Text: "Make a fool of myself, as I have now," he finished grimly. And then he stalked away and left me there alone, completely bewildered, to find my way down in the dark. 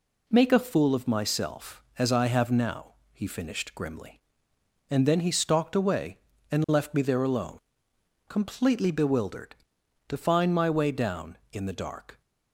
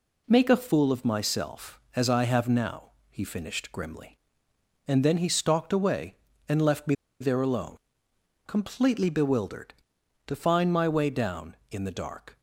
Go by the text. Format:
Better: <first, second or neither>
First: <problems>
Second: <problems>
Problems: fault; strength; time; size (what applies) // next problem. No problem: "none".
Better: first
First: none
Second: pauses between "me" and "there"; slight; at 6.9 s; 0.26 s long